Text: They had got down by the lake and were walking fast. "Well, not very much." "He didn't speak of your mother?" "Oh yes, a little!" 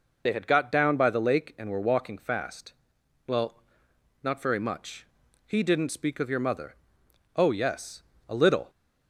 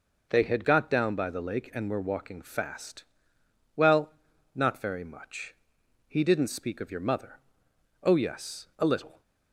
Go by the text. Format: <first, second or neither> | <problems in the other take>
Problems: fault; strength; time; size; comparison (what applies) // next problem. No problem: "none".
second | loses the start of "They"; at 0.2 s; 35 ms